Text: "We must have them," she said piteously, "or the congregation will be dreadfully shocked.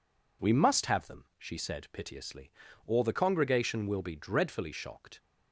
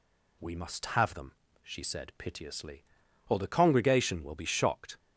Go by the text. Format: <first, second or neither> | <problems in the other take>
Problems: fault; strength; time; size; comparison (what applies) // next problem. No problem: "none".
first | skips "dreadfully"; at 4.4 s